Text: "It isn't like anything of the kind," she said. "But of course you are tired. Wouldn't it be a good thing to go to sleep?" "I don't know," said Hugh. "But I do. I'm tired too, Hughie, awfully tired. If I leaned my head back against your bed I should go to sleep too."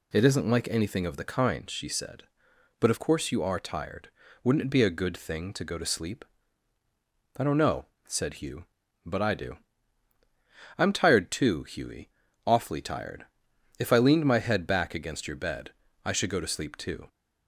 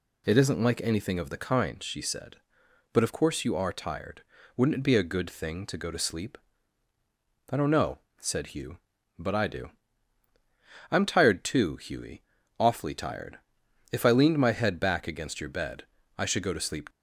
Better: first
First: pauses between "bed" and "I"; slight; at 15.7 s; 0.32 s long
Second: pauses between "bed" and "I"; slight; at 15.8 s; 0.32 s long // stops before "too"; at 16.8 s

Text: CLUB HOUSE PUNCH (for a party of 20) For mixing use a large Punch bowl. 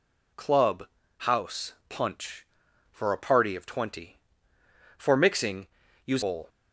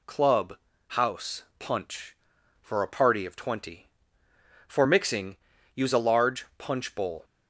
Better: second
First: pauses between "CLUB" and "HOUSE"; slight; at 0.8 s; 0.32 s long // pauses between "mixing" and "use"; at 5.6 s; 0.40 s long // skips "a large Punch"; at 6.2 s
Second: pauses between "CLUB" and "HOUSE"; slight; at 0.5 s; 0.32 s long // pauses between "mixing" and "use"; at 5.3 s; 0.40 s long

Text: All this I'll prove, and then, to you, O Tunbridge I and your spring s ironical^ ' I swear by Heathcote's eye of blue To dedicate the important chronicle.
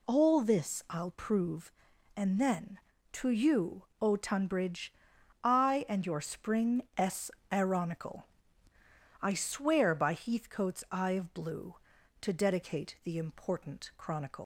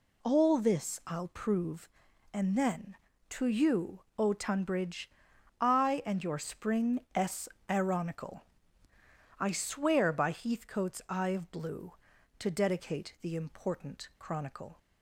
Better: second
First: pauses between "Tunbridge" and "I"; noticeable; at 4.9 s; 0.50 s long // pauses between "s" and "ironical"; slight; at 7.3 s; 0.22 s long // leaves "chronicle" unfinished; at 14.4 s; 120 ms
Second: pauses between "Tunbridge" and "I"; noticeable; at 5.0 s; 0.50 s long // pauses between "s" and "ironical"; slight; at 7.4 s; 0.22 s long

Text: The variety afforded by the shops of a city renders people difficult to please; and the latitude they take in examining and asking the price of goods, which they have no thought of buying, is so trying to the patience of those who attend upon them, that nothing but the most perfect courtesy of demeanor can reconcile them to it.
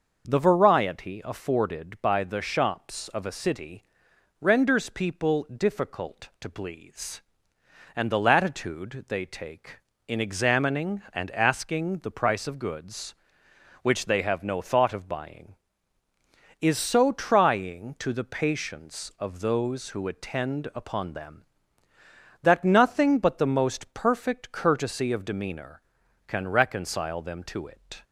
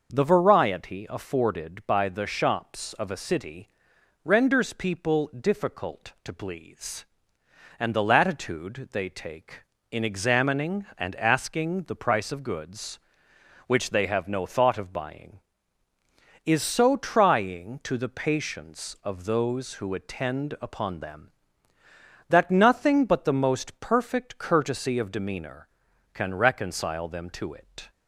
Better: neither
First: starts louder than the rest; noticeable; until 1.3 s; 6 dB // pauses between "city" and "renders"; noticeable; at 3.8 s; 0.56 s long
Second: starts louder than the rest; noticeable; until 1.1 s; 6 dB // pauses between "city" and "renders"; noticeable; at 3.6 s; 0.54 s long

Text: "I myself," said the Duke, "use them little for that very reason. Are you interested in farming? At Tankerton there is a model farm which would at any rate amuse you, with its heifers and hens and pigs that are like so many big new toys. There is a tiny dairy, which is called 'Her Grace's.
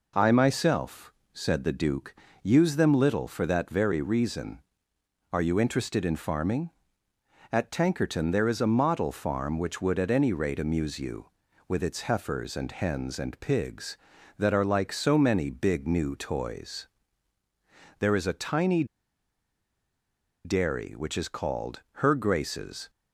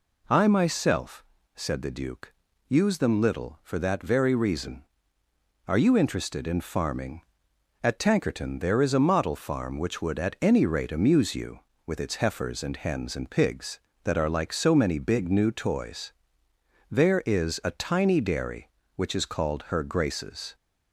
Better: second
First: pauses between "tiny" and "dairy"; strong; at 18.8 s; 1.6 s long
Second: none

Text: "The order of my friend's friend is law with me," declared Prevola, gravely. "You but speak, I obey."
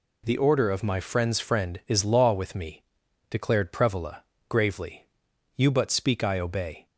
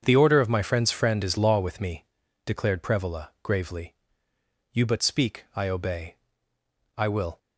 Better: first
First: none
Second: starts louder than the rest; strong; until 1.0 s; 7.5 dB // goes on to say "I will"; slight; from 6.9 s on; 0.40 s long

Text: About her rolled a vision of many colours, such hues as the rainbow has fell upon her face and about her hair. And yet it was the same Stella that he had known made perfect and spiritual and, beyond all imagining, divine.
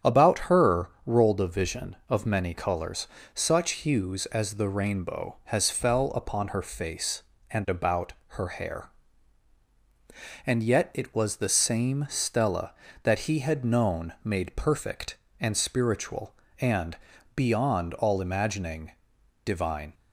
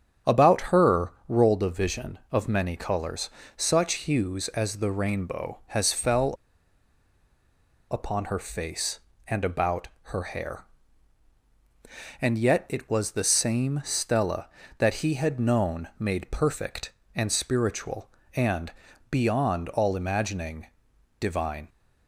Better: first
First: starts louder than the rest; strong; until 1.3 s; 8.5 dB // pauses between "her" and "rolled"; slight; at 0.8 s; 0.18 s long // pauses between "about" and "her"; slight; at 8.1 s; 0.16 s long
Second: starts louder than the rest; strong; until 1.5 s; 8.5 dB // pauses between "her" and "rolled"; slight; at 1.1 s; 0.18 s long // pauses between "fell" and "upon"; strong; at 6.3 s; 1.5 s long // pauses between "about" and "her"; slight; at 9.8 s; 0.16 s long

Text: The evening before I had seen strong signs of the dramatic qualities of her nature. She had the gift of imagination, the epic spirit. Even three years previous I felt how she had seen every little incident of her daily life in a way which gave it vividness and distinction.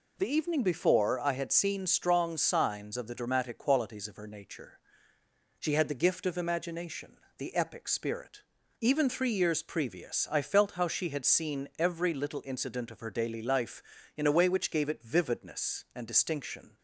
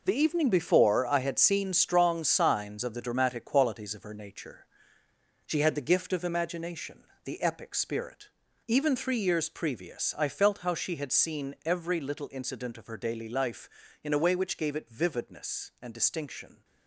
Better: first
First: none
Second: gets quieter; strong; throughout; 9.5 dB

